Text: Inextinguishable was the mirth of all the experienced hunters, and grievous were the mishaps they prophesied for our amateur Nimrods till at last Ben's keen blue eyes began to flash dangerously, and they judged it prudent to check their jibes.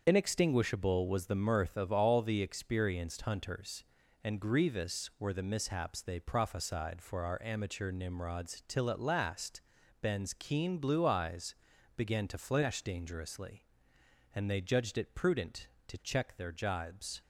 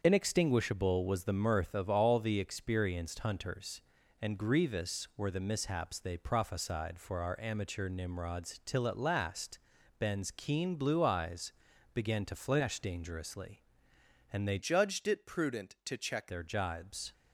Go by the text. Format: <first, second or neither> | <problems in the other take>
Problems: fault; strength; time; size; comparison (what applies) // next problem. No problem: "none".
first | starts louder than the rest; until 1.0 s; 7 dB; also in the first // pauses between "last" and "Ben's"; at 9.5 s; 0.40 s long; also in the first // pauses between "eyes" and "began"; at 11.5 s; 0.42 s long; also in the first // changes voice from "judged" to "check"; from 14.5 to 16.3 s; 1.8 s long